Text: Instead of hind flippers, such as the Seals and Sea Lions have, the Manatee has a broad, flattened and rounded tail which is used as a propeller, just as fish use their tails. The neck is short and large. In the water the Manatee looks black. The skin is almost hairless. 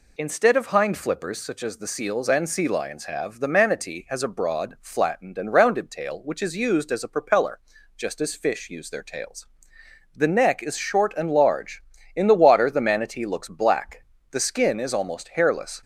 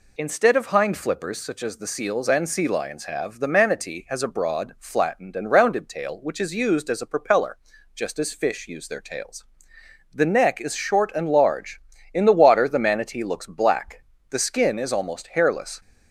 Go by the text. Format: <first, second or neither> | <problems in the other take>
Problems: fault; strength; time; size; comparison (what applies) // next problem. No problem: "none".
neither | none